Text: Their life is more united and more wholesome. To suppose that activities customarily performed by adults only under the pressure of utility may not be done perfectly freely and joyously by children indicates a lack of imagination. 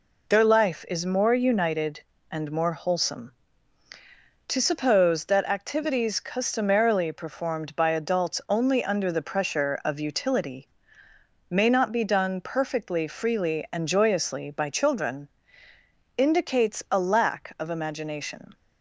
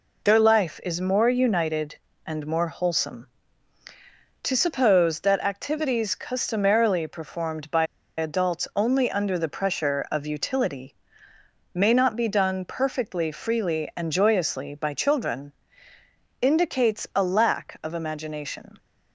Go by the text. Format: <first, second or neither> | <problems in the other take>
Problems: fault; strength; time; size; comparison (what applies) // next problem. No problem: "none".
first | pauses between "by" and "adults"; slight; at 7.8 s; 0.32 s long // pauses between "utility" and "may"; noticeable; at 10.9 s; 0.78 s long; noticeable in the first // pauses between "children" and "indicates"; noticeable; at 15.5 s; 0.86 s long; noticeable in the first